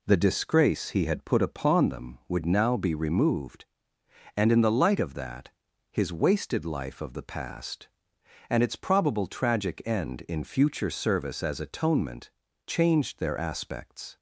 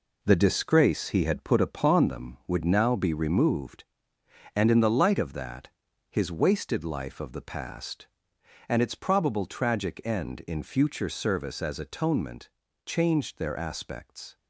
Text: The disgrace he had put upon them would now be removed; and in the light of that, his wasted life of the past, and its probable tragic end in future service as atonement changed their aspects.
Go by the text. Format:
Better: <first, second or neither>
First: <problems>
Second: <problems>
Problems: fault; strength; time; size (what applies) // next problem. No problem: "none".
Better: first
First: pauses between "atonement" and "changed"; slight; at 12.3 s; 0.36 s long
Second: gets quieter; strong; throughout; 7 dB // pauses between "atonement" and "changed"; slight; at 12.4 s; 0.36 s long